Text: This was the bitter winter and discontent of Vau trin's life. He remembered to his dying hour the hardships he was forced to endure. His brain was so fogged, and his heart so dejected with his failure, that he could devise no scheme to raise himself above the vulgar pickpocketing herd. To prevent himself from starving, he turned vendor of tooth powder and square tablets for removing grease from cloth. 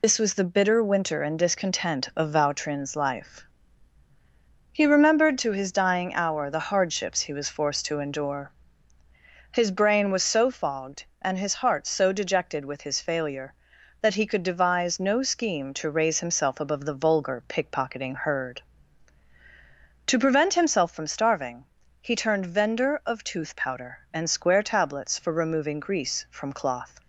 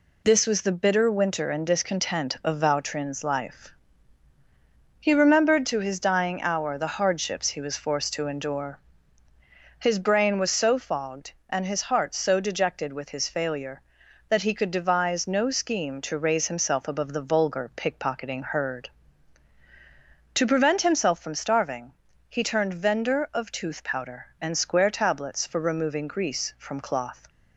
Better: second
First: loses the start of "This"; at 0.0 s; 70 ms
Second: none

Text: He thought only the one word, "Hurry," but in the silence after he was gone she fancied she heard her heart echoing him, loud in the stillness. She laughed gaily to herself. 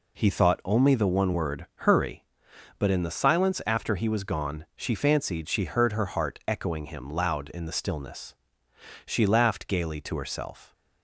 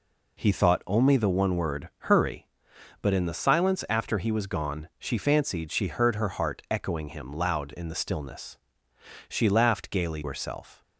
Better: first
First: none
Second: skips "to"; at 10.2 s

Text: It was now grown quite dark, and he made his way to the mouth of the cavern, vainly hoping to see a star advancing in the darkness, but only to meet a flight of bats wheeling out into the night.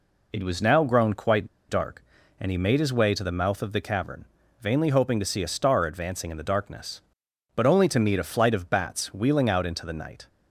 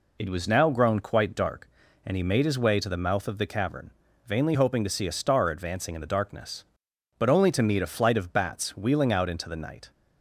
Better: second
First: pauses between "quite" and "dark"; slight; at 1.4 s; 0.21 s long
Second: none

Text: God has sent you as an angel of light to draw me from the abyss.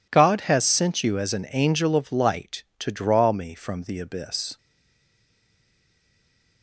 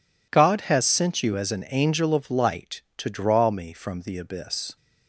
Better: second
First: stays silent after the last word; noticeable; from 4.5 s on; 2.1 s long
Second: none

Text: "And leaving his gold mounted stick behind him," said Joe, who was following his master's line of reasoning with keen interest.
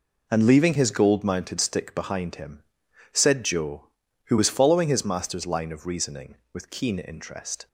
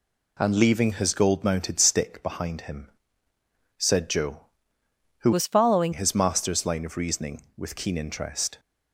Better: first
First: none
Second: changes voice from "was" to "following"; from 5.3 to 5.9 s; 0.6 s long

